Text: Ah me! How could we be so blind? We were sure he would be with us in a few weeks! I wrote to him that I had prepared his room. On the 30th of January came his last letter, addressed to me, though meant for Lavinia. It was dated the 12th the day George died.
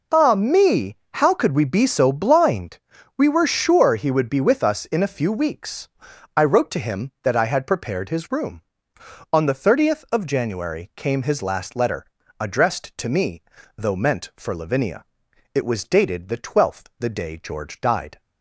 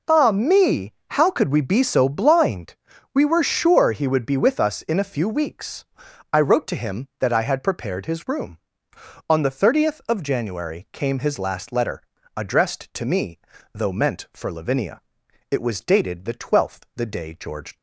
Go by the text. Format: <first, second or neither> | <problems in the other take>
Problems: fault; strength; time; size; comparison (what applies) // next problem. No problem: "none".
first | stops before "died"; at 17.7 s